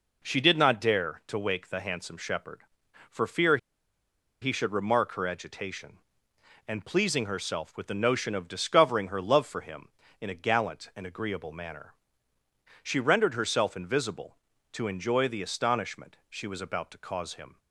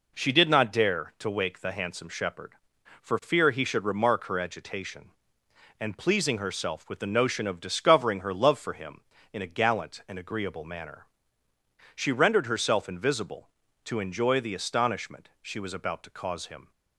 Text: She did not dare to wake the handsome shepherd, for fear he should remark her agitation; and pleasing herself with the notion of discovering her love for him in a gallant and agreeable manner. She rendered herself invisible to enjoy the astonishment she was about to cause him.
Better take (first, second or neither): second